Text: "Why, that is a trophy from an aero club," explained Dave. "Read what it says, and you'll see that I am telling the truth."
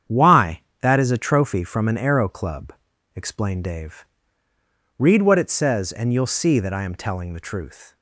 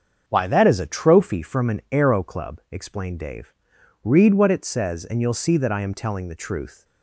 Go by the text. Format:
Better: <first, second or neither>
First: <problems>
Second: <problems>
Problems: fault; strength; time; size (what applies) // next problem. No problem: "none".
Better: neither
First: starts louder than the rest; strong; until 1.3 s; 8.5 dB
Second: starts louder than the rest; until 1.2 s; 7 dB